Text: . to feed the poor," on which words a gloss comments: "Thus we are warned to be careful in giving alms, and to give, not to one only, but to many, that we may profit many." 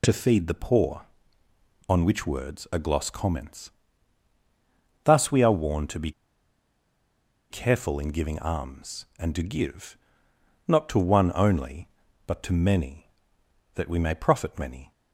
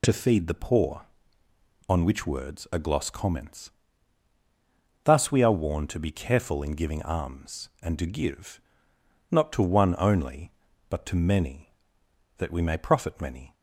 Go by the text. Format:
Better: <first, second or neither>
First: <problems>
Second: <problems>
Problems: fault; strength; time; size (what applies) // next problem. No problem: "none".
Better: second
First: pauses between "be" and "careful"; strong; at 6.1 s; 1.3 s long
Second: none